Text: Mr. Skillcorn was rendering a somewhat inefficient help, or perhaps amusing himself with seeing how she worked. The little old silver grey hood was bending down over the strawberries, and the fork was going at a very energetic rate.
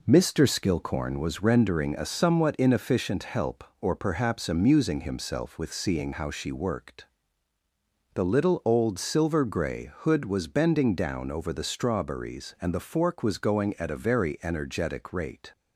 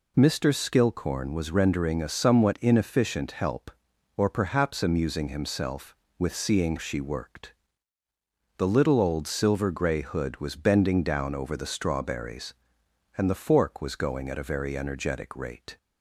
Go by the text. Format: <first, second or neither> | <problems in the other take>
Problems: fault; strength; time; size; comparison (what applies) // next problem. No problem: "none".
first | skips "how"; at 6.7 s